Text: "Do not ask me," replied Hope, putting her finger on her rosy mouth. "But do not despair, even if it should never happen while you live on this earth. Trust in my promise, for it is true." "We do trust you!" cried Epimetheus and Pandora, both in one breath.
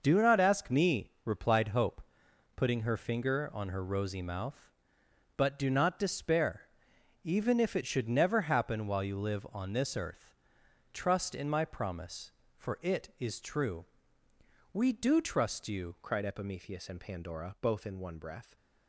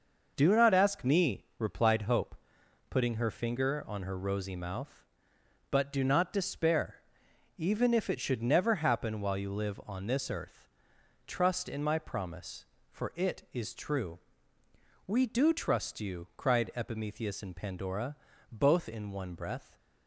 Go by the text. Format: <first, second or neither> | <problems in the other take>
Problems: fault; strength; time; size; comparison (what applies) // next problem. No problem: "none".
second | changes voice at "cried"; from 16.0 s on; 2.5 s long